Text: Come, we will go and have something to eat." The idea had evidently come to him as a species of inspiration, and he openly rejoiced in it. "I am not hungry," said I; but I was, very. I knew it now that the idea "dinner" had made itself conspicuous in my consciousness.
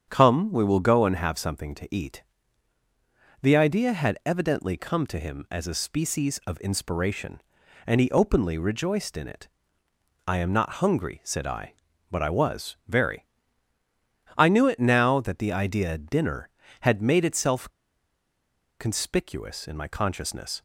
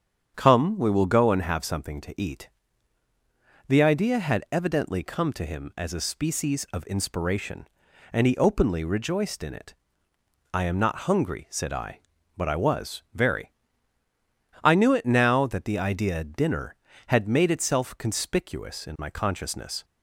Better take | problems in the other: second | starts louder than the rest; strong; until 1.0 s; 8 dB; strong in the second // pauses between "itself" and "conspicuous"; at 17.7 s; 1.0 s long

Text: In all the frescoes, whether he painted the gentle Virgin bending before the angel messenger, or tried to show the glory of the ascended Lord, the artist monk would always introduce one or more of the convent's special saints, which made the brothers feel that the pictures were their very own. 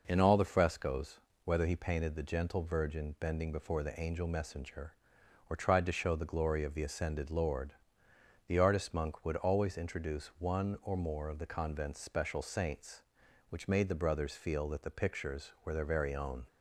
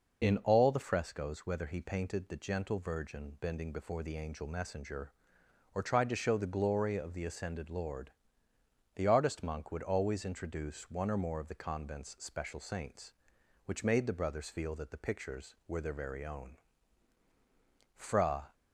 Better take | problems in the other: first | goes on to say "Fra"; from 17.9 s on; 0.56 s long

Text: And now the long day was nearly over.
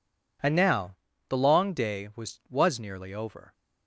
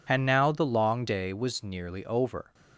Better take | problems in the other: second | pauses between "now" and "the"; slight; at 0.9 s; 0.32 s long // says "was" twice; at 2.4 s

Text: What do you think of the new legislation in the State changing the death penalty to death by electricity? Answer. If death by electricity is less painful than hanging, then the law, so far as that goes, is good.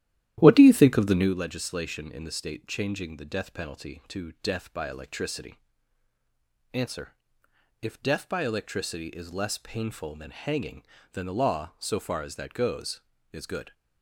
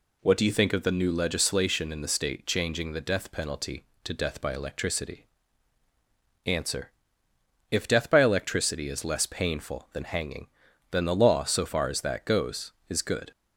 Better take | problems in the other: second | starts louder than the rest; strong; until 1.3 s; 12.5 dB

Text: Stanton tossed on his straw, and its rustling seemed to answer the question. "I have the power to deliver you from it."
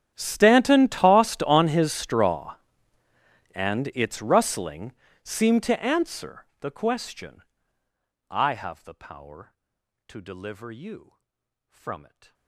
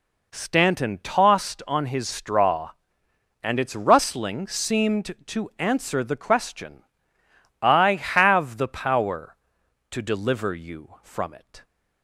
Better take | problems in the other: second | gets quieter; strong; throughout; 29.5 dB // pauses between "rustling" and "seemed"; slight; at 4.9 s; 0.30 s long

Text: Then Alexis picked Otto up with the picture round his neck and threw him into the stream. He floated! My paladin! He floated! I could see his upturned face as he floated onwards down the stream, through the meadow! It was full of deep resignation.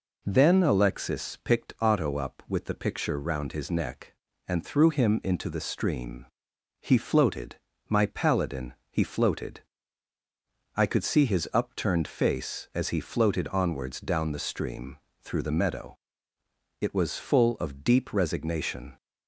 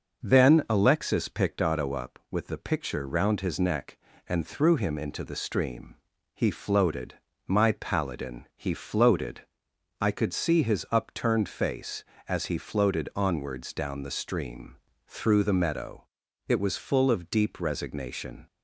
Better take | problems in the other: neither | none

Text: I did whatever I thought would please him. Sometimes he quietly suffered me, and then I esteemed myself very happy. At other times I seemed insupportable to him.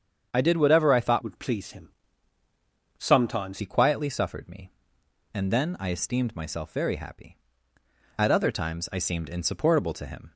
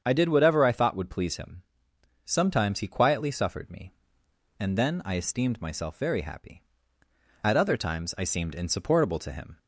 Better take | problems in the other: second | starts louder than the rest; strong; until 1.3 s; 7.5 dB; strong in the second // changes voice from "would" to "Sometimes"; from 1.2 to 3.5 s; 2.3 s long

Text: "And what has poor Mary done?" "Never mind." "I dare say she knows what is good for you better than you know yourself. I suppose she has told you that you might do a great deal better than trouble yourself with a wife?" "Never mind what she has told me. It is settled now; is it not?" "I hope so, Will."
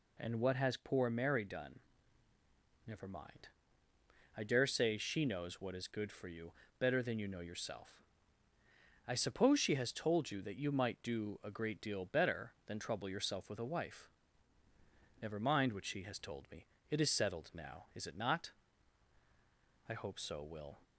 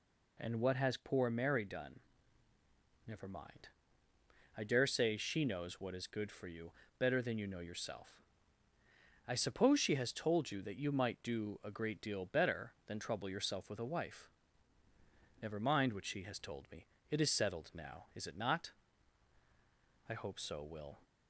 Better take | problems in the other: neither | pauses between "you" and "better"; slight; the same in both

